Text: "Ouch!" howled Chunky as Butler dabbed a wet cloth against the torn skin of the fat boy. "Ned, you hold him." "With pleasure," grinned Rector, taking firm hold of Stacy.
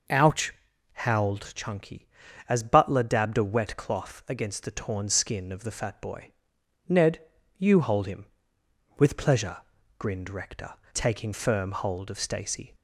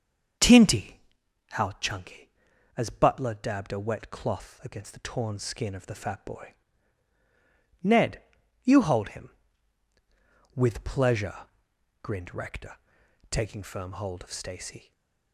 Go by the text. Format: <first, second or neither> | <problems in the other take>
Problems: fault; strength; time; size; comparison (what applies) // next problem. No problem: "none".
first | starts louder than the rest; until 1.9 s; 7 dB // says "Tinty" for "Ouch"; at 0.3 s // stays silent after the last word; slight; from 14.7 s on; 0.6 s long